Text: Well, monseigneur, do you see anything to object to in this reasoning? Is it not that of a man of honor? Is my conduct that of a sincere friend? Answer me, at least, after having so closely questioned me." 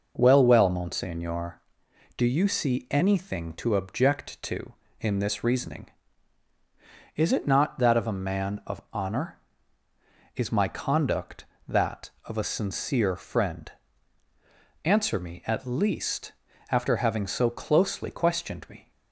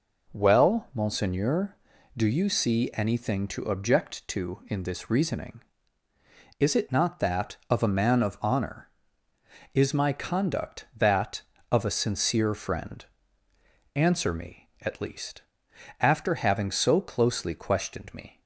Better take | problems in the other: second | says "Well" twice; at 0.4 s

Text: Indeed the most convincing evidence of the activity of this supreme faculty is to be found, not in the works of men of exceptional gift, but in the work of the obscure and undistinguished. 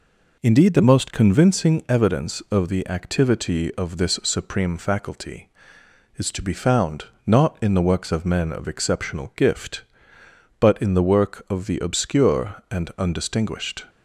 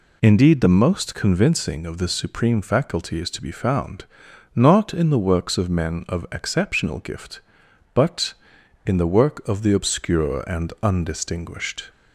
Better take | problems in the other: first | skips "evidence of the activity"; at 1.8 s

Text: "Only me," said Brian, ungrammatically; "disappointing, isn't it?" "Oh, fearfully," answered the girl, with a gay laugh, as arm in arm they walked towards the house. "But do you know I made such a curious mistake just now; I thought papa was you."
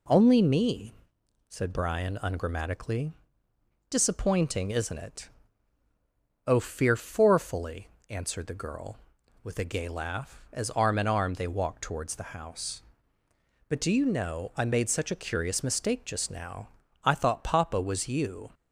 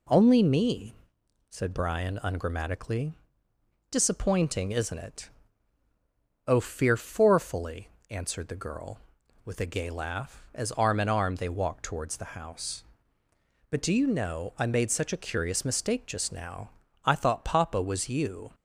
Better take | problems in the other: neither | none

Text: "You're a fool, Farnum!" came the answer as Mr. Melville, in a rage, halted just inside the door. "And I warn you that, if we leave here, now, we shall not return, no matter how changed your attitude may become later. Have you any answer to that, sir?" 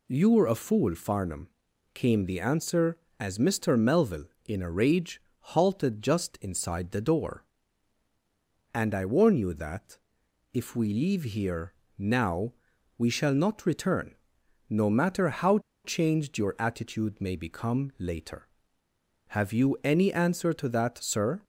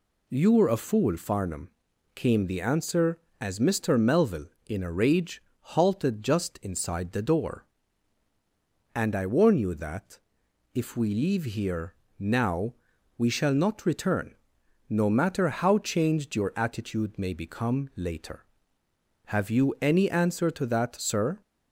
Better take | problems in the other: second | pauses between "how" and "changed"; slight; at 15.5 s; 0.27 s long

